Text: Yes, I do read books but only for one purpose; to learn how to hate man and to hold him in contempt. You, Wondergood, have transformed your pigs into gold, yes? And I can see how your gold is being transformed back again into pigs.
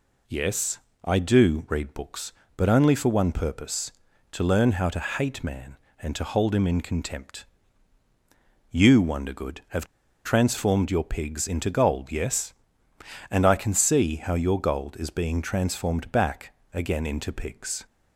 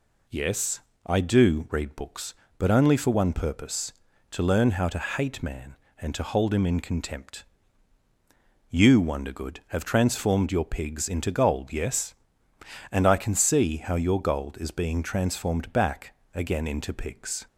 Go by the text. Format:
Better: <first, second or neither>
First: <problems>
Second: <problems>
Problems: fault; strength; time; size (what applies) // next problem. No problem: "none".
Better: second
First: pauses between "have" and "transformed"; at 9.8 s; 0.39 s long // pauses between "back" and "again"; slight; at 16.5 s; 0.20 s long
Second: pauses between "back" and "again"; slight; at 16.1 s; 0.20 s long